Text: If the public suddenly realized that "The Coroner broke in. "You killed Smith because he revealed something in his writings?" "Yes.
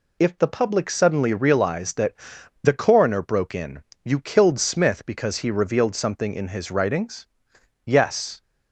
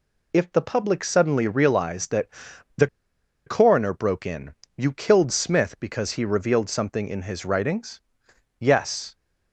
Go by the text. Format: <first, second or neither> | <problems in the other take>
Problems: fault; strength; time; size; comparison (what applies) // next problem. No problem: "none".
first | pauses between "that" and "The"; noticeable; at 2.2 s; 0.48 s long; noticeable in the first // pauses between "The" and "Coroner"; noticeable; at 2.8 s; 0.60 s long